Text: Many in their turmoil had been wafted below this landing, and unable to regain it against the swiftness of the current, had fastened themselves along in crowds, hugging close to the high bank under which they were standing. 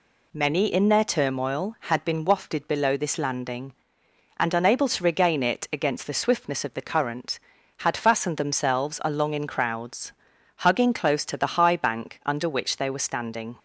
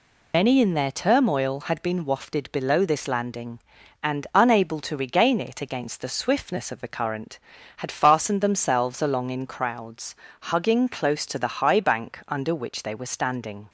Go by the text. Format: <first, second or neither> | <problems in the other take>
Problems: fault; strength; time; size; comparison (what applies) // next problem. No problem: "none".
first | loses the start of "Many"; at 0.3 s; 90 ms